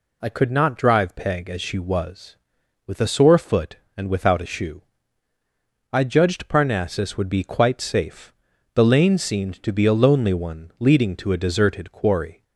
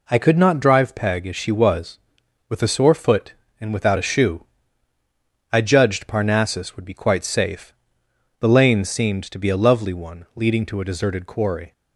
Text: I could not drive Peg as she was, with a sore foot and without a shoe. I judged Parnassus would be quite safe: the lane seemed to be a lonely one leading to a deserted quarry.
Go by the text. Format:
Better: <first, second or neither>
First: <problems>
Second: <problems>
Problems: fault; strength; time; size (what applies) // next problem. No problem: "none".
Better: first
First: none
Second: says "lovely" for "lonely"; at 9.5 s